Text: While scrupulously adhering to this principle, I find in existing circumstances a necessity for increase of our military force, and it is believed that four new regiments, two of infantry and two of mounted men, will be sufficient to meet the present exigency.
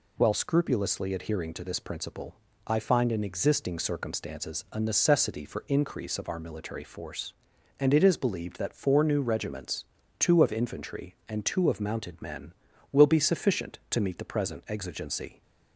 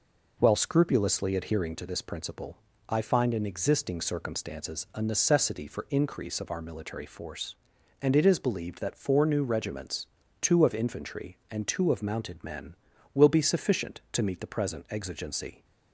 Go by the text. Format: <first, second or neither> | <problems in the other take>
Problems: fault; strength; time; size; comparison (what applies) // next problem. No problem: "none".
first | starts louder than the rest; noticeable; until 1.9 s; 4.5 dB